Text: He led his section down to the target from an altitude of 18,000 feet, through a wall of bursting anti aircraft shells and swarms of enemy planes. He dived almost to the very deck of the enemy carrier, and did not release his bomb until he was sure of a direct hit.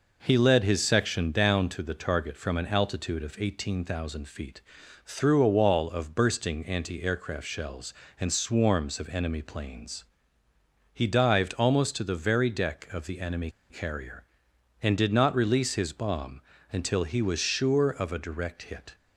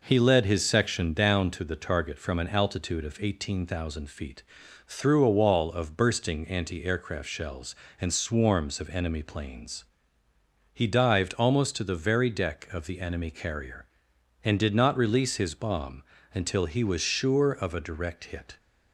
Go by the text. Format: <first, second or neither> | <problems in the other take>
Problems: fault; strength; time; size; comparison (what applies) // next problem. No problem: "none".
second | pauses between "enemy" and "carrier"; slight; at 13.4 s; 0.20 s long // pauses between "bomb" and "until"; slight; at 16.3 s; 0.32 s long; slight in the second